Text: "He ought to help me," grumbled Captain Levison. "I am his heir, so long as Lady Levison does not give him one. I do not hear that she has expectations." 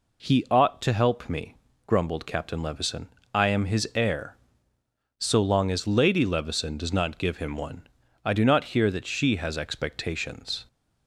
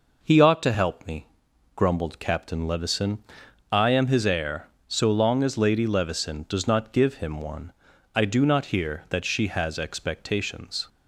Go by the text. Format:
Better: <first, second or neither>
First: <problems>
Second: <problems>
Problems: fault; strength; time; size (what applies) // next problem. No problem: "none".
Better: neither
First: none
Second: none